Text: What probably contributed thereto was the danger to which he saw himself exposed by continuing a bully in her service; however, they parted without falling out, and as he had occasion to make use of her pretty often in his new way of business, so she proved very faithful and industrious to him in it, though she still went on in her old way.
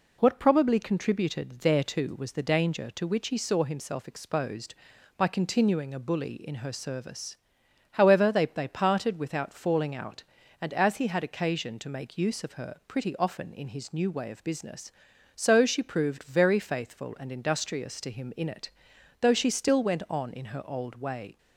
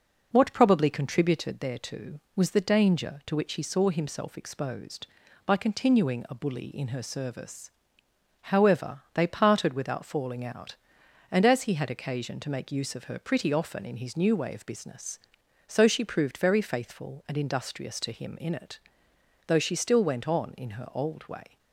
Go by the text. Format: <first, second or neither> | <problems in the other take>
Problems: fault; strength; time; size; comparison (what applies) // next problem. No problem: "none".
second | says "they" twice; at 8.4 s